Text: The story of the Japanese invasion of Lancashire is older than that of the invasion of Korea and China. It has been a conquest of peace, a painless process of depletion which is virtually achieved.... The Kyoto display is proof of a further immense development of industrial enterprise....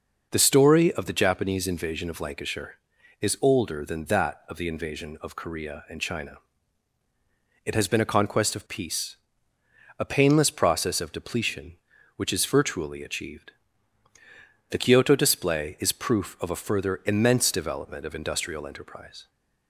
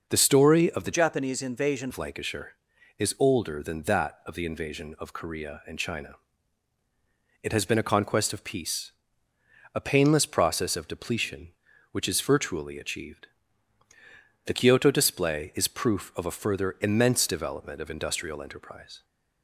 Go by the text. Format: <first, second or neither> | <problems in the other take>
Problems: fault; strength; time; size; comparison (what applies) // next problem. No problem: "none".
first | changes voice from "Japanese" to "invasion"; from 0.9 to 1.8 s; 0.9 s long